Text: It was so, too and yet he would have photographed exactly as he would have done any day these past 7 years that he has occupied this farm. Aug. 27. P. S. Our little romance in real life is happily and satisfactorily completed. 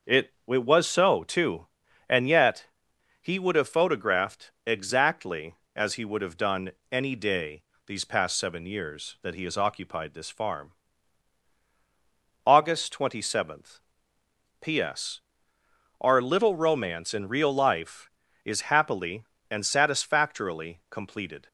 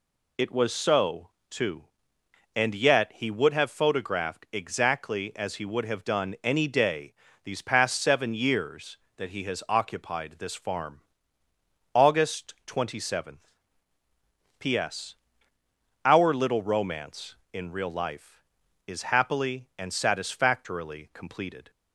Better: second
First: starts louder than the rest; until 1.2 s; 6.5 dB // says "It" twice; at 0.4 s // pauses between "yet" and "he"; noticeable; at 2.6 s; 0.56 s long // pauses between "done" and "any"; slight; at 6.7 s; 0.20 s long // pauses between "day" and "these"; slight; at 7.6 s; 0.26 s long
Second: pauses between "day" and "these"; slight; at 7.1 s; 0.30 s long

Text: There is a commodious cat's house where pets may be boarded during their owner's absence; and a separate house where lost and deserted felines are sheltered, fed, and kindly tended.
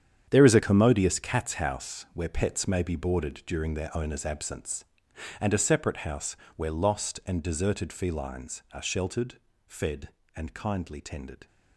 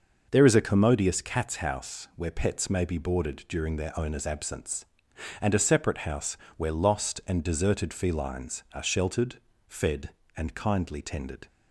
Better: second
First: gets quieter; strong; throughout; 12 dB // starts louder than the rest; strong; until 1.3 s; 9 dB // pauses between "house" and "where"; slight; at 6.3 s; 0.22 s long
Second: starts louder than the rest; noticeable; until 1.3 s; 6 dB // pauses between "house" and "where"; slight; at 6.3 s; 0.22 s long

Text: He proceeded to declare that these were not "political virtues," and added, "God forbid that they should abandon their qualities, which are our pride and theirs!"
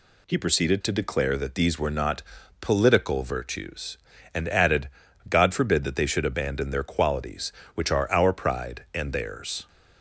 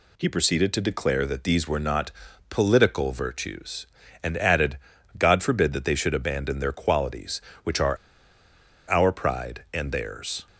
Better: first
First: pauses between "not" and "political"; at 2.2 s; 0.38 s long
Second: pauses between "not" and "political"; at 2.1 s; 0.38 s long // pauses between "are" and "our"; noticeable; at 7.9 s; 0.93 s long

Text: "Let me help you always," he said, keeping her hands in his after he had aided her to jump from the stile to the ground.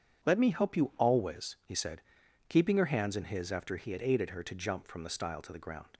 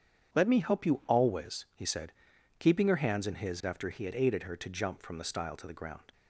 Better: neither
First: starts louder than the rest; strong; until 1.3 s; 8.5 dB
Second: starts louder than the rest; strong; until 1.3 s; 8.5 dB

